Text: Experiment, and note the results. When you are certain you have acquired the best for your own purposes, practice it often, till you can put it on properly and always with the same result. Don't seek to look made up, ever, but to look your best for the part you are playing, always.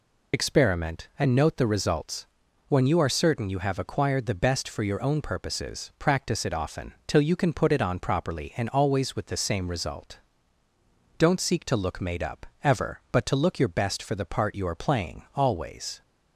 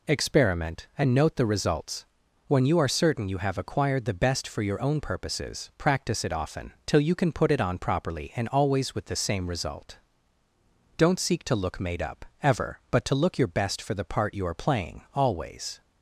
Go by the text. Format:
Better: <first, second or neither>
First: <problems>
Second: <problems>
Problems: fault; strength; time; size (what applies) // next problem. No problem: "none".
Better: second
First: loses the start of "Experiment"; at 0.3 s; 55 ms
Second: none